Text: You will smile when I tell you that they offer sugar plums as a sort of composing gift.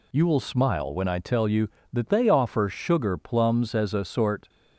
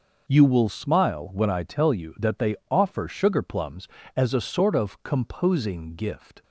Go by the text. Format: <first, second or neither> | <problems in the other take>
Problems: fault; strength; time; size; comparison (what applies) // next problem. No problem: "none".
second | stops before "of composing gift"; at 4.4 s